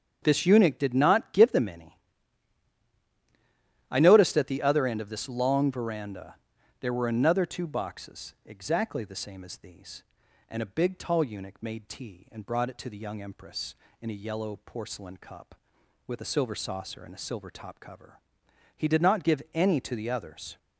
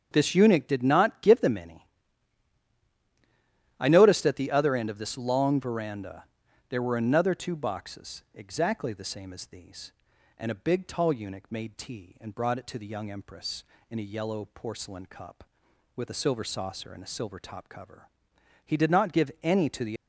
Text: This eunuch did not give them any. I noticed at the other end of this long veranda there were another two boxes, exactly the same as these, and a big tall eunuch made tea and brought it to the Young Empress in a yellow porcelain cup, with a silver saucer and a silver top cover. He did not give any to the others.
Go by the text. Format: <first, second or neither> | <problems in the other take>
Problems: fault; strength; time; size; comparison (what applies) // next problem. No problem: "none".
first | starts louder than the rest; strong; until 1.1 s; 7.5 dB; strong in the first // pauses between "veranda" and "there"; at 6.2 s; 0.44 s long; also in the first // stops before "others"; at 19.9 s